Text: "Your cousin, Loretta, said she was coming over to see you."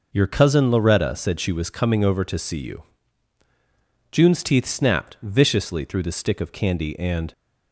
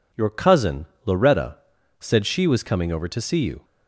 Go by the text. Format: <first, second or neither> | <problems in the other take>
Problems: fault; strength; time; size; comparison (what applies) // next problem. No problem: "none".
second | goes on to say "June's teeth snapped viciously through the stick of candy and"; strong; from 4.0 s on; 3.2 s long